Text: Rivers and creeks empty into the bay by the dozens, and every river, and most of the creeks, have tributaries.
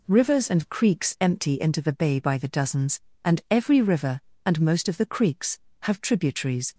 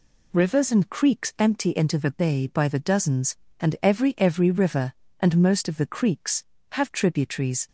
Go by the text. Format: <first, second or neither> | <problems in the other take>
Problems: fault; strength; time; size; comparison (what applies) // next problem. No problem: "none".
first | says "every" twice; at 4.1 s